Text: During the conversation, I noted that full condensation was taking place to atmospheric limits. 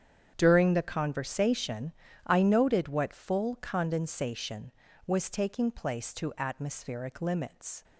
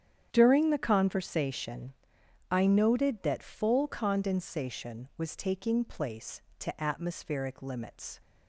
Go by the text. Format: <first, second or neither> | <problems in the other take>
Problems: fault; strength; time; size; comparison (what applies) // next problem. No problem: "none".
second | starts louder than the rest; strong; until 1.3 s; 8.5 dB; strong in the second // says "what" for "that"; at 2.8 s